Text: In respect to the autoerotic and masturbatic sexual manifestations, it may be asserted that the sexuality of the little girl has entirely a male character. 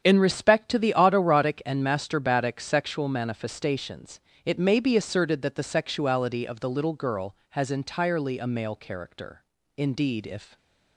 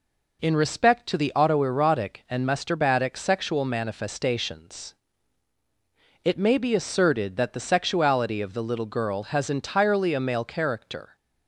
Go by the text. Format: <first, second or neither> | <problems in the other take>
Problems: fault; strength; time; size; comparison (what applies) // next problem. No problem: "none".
second | starts louder than the rest; strong; until 1.0 s; 8.5 dB // goes on to say "Indeed if"; noticeable; from 9.7 s on; 0.80 s long // stays silent after the last word; slight; from 10.4 s on; 0.5 s long